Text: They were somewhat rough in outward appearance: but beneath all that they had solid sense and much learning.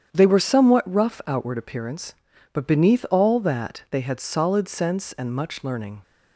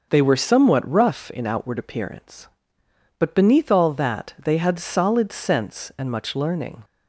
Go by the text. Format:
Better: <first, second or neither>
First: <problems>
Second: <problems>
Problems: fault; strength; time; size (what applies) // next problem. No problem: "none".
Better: second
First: starts louder than the rest; strong; until 1.1 s; 8.5 dB // skips "in"; at 1.2 s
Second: none